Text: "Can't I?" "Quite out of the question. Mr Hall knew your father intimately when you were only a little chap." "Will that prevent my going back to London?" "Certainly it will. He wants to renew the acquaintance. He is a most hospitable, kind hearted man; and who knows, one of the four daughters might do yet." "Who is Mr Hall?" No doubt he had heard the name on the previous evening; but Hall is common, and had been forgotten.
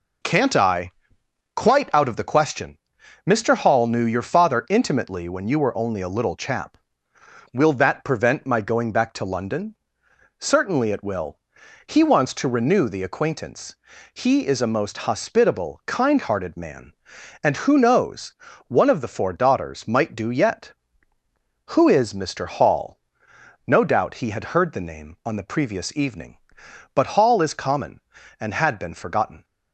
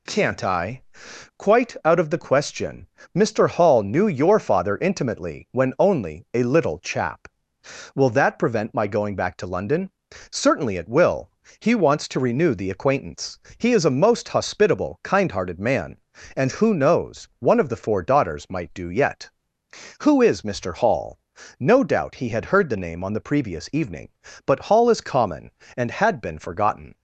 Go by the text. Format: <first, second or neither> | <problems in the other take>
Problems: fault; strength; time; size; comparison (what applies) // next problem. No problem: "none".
first | skips "you were"; at 5.7 s